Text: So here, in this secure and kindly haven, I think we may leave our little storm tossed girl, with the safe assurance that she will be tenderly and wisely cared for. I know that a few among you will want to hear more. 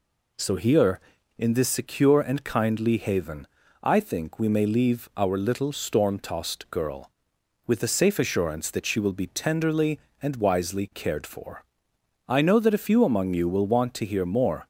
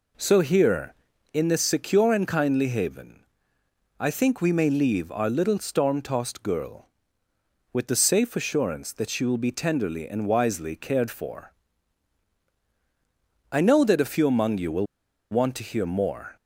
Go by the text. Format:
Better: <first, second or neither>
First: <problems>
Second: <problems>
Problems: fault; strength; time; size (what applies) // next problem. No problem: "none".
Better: first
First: none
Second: pauses between "will" and "want"; at 14.8 s; 0.45 s long